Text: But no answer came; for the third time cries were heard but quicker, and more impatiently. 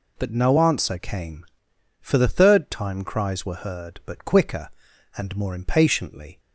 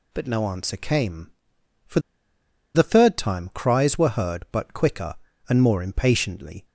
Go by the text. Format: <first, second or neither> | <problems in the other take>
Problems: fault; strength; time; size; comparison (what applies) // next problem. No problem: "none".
first | pauses between "for" and "the"; noticeable; at 1.9 s; 0.75 s long